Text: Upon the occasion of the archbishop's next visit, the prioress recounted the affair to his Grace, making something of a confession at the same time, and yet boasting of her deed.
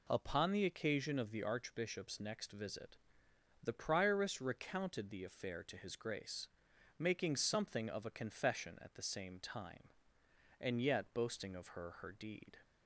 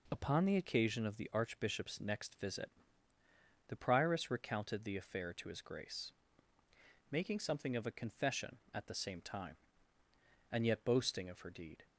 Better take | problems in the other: second | says "her" twice; at 11.9 s

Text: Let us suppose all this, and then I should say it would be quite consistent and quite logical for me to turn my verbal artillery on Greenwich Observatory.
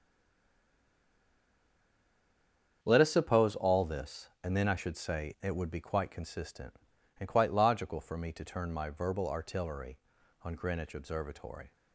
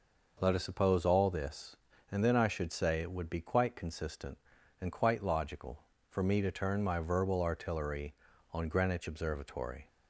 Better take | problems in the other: second | stays silent before the first word; strong; until 2.8 s; 2.8 s long // starts louder than the rest; strong; until 3.8 s; 8 dB

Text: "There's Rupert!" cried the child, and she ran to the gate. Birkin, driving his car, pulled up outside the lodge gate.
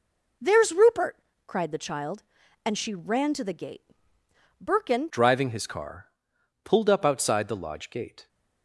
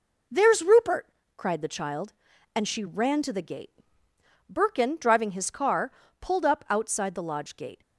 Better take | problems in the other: second | changes voice at "driving"; from 5.0 s on; 3.2 s long

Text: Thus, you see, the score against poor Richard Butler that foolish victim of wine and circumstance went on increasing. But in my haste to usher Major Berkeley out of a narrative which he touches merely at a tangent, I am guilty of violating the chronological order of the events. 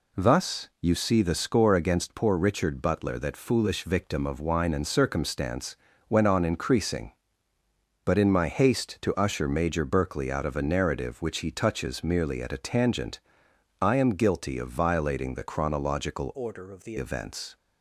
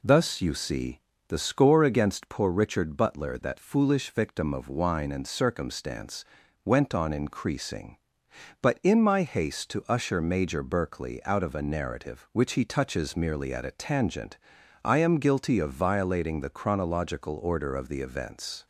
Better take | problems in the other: second | pauses between "circumstance" and "went"; slight; at 5.7 s; 0.32 s long; also in the second // changes voice from "order" to "the"; from 16.3 to 16.9 s; 0.6 s long

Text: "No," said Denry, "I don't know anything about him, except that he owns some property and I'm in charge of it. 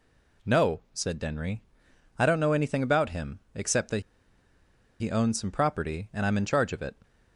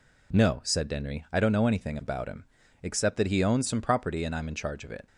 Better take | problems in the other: second | pauses between "that" and "he"; at 4.0 s; 0.99 s long

